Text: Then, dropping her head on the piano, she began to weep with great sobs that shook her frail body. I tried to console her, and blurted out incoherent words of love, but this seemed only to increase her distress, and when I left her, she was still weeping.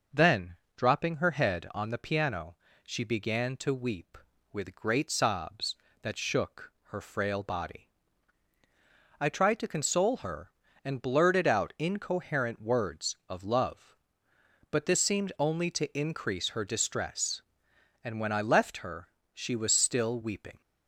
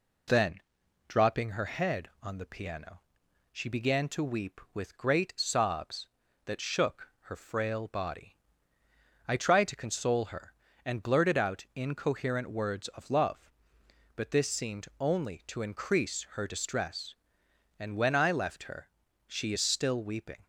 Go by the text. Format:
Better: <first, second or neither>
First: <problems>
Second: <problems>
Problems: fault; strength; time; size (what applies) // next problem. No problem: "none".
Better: first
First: none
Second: says "is" for "was"; at 19.5 s